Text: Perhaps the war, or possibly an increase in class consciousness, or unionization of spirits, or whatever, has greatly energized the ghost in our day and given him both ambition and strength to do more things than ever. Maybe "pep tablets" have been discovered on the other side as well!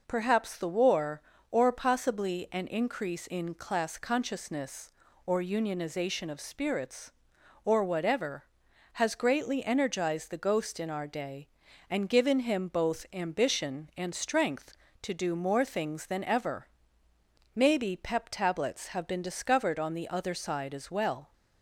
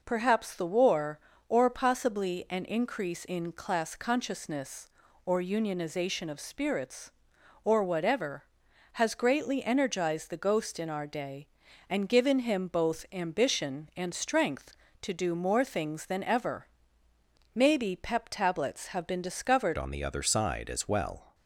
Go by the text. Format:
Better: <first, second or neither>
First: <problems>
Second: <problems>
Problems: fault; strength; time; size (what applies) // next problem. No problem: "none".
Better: first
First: none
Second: changes voice at "on"; from 19.7 s on; 1.6 s long